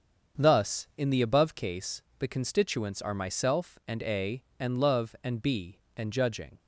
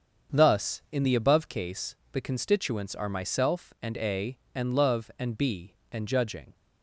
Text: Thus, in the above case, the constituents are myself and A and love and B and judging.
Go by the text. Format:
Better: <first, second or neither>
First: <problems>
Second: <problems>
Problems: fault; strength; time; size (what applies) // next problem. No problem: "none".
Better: neither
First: starts louder than the rest; strong; until 1.5 s; 7 dB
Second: starts louder than the rest; until 1.4 s; 7 dB